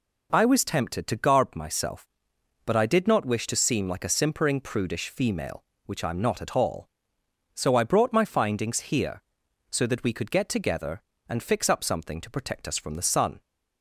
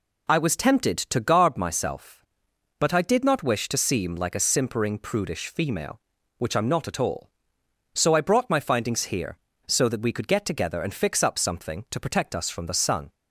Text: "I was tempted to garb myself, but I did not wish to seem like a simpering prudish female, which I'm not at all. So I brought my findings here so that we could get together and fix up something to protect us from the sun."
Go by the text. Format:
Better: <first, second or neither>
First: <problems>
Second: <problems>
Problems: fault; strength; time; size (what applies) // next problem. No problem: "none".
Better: neither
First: none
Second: none